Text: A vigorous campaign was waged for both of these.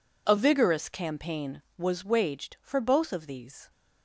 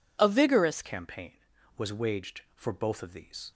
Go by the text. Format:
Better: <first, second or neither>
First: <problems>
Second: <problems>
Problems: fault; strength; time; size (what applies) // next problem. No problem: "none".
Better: first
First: none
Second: changes voice at "campaign"; from 0.8 s on; 2.7 s long